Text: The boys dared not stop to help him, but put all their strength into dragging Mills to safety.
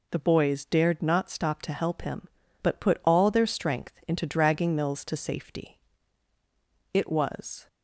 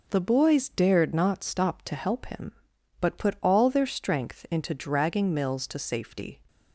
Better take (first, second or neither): second